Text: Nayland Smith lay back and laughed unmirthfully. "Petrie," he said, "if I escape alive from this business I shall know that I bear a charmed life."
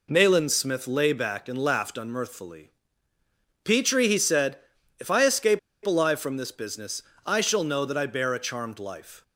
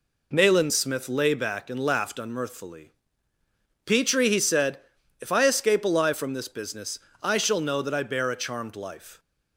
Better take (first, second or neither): second